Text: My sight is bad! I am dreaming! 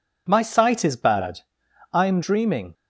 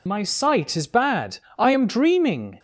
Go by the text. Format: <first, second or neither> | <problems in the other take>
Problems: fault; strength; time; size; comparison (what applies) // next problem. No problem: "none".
first | loses the start of "My"; at 0.0 s; 60 ms